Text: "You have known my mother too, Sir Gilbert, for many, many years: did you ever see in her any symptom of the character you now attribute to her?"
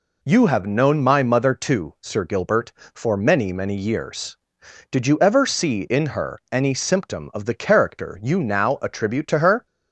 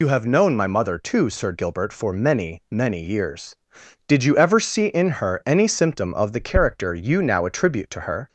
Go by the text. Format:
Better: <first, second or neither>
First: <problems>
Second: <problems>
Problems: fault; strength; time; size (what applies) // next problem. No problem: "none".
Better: first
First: none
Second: loses the start of "You"; at 0.0 s; 65 ms